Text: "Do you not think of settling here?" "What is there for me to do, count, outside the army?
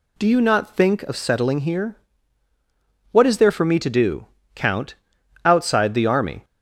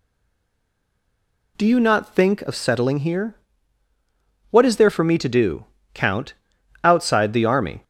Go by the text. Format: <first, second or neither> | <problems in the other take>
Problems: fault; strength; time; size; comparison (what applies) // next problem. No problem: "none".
first | stays silent before the first word; noticeable; until 1.5 s; 1.5 s long